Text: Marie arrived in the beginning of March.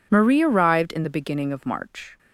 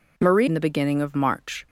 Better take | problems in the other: first | skips "arrived"; at 0.4 s

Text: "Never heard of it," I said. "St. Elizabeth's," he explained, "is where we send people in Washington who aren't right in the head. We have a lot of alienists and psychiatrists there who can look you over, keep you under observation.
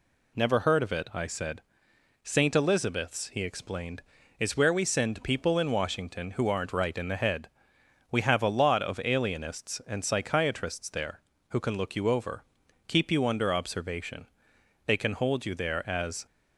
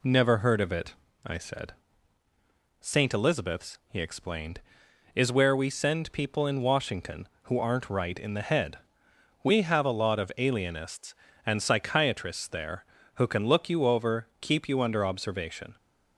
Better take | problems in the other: second | goes on to say "They can hold you there as"; from 14.8 s on; 1.4 s long

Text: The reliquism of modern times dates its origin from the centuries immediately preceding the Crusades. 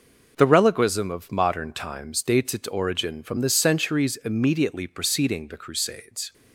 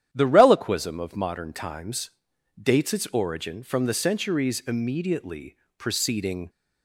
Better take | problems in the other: first | starts louder than the rest; strong; until 1.1 s; 10 dB // pauses between "times" and "dates"; noticeable; at 2.0 s; 0.52 s long // pauses between "immediately" and "preceding"; slight; at 5.5 s; 0.22 s long // stops before "the Crusades"; at 6.4 s

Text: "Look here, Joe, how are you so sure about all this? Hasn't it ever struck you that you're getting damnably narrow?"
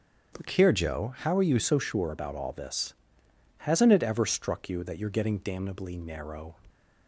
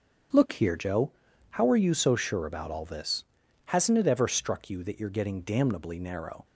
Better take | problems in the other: second | starts louder than the rest; strong; until 1.4 s; 7.5 dB; strong in the second // changes voice from "here" to "you"; from 0.5 to 1.5 s; 1.0 s long

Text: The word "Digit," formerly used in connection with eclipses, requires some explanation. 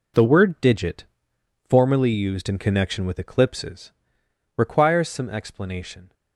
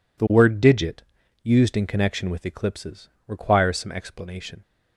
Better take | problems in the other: first | skips "formerly"; at 1.2 s

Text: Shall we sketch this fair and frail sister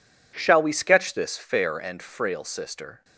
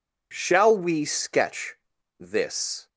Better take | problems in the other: first | pauses between "sketch" and "this"; at 1.7 s; 0.44 s long // stops before "fair and frail sister"; at 2.8 s

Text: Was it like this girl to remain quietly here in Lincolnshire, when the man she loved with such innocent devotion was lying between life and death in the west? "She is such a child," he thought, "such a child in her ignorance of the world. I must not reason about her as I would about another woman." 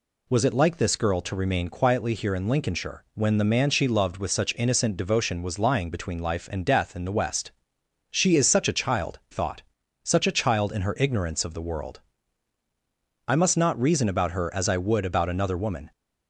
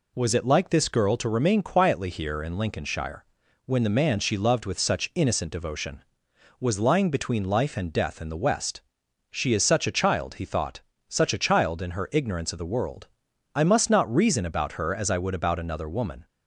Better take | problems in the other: second | skips "he"; at 9.2 s

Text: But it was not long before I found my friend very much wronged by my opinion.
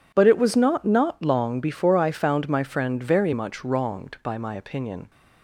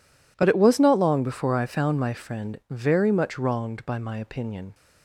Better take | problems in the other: second | says "not" twice; at 0.8 s

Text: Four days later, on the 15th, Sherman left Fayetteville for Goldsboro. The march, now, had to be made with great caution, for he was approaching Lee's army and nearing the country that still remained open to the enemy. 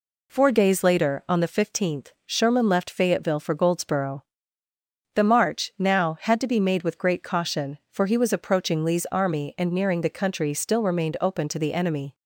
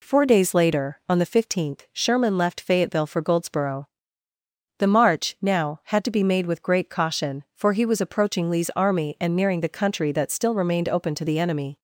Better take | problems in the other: second | skips "that"; at 10.5 s

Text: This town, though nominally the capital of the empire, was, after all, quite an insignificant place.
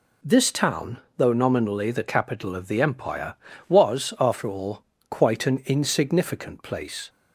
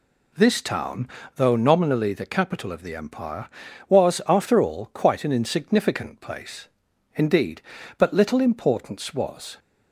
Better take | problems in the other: first | goes on to say "Indeed but little importance was"; strong; from 7.1 s on; 2.4 s long

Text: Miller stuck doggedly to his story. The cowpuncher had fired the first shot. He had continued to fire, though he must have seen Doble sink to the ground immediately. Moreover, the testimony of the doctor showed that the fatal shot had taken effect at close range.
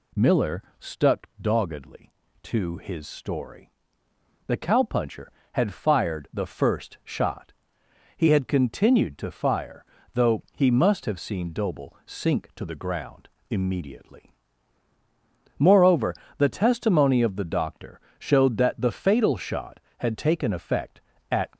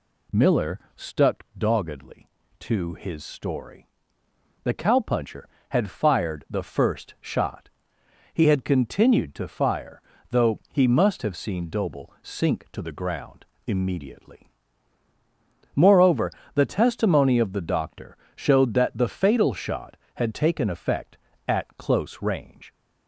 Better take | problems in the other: second | pauses between "Miller" and "stuck"; slight; at 0.6 s; 0.16 s long; slight in the second // pauses between "ground" and "immediately"; slight; at 13.2 s; 0.22 s long; slight in the second // pauses between "doctor" and "showed"; slight; at 17.9 s; 0.18 s long; slight in the second // stops before "close range"; at 21.5 s

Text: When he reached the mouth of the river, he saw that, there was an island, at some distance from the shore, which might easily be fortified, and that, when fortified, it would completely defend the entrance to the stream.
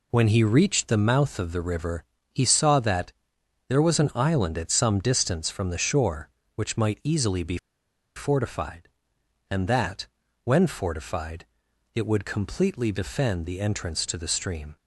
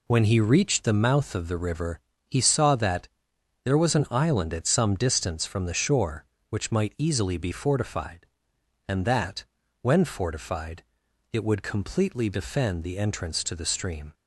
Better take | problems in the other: second | pauses between "be" and "fortified"; noticeable; at 7.5 s; 0.58 s long

